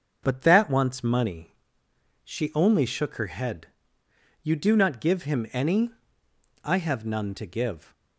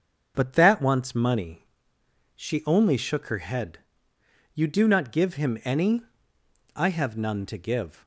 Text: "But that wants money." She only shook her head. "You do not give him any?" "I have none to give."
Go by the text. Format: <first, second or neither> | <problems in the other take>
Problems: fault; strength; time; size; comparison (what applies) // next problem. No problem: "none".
neither | starts louder than the rest; the same in both